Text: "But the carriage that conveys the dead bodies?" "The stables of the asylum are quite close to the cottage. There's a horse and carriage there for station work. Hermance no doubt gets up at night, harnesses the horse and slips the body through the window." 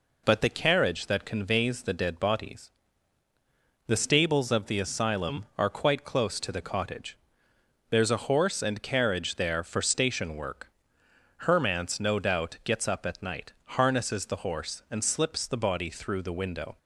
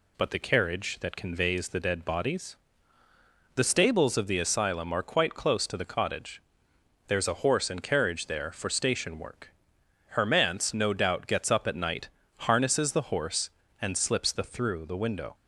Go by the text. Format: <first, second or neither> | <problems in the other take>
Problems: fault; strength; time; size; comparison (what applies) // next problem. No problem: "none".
first | skips "body"; at 14.4 s